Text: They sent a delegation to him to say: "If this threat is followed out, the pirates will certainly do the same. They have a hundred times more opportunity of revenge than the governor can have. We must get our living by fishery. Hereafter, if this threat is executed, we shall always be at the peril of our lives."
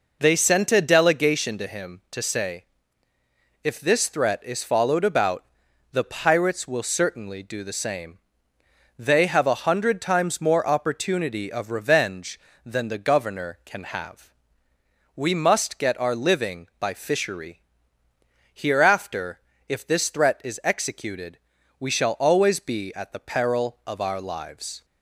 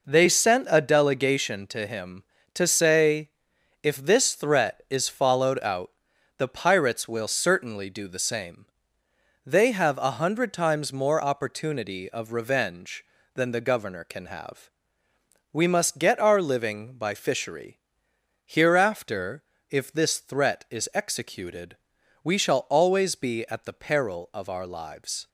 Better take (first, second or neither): second